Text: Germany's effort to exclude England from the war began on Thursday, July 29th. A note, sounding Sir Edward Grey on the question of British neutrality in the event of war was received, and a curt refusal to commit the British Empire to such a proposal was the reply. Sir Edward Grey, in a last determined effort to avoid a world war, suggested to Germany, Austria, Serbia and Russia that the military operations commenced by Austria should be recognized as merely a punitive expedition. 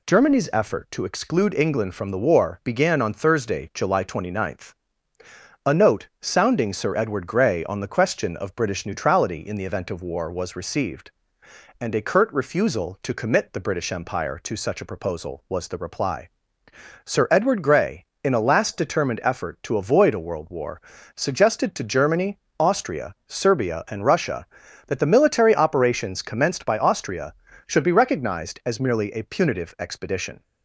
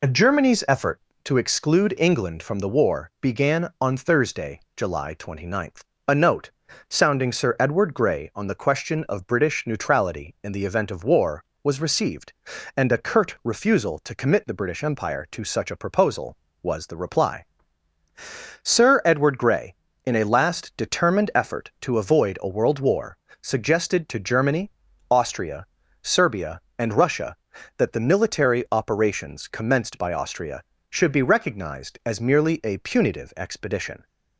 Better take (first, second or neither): neither